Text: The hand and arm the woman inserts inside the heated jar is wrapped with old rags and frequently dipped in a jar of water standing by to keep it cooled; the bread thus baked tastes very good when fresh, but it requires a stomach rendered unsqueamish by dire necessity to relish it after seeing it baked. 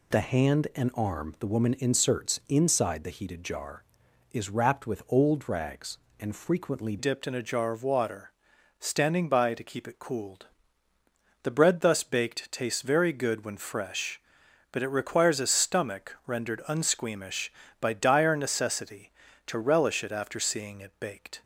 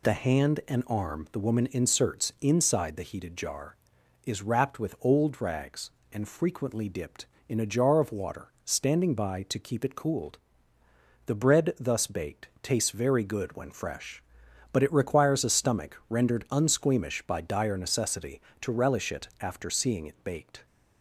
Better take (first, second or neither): second